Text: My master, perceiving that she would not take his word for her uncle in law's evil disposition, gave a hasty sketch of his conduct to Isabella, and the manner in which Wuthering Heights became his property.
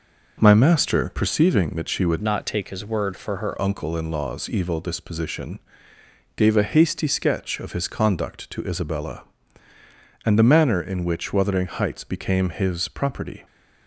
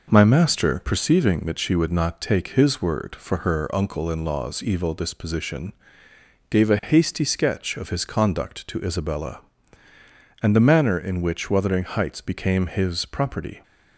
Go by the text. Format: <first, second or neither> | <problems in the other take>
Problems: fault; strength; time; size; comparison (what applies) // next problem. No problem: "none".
second | changes voice from "not" to "her"; from 2.2 to 3.5 s; 1.3 s long